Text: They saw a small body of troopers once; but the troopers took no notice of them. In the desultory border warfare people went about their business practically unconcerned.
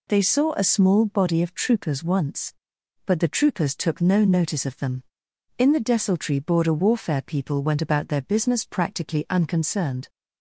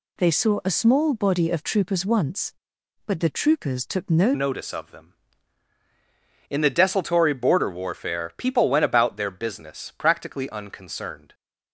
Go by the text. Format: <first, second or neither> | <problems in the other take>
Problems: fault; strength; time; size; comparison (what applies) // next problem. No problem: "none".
first | changes voice at "notice"; from 4.3 s on; 7.0 s long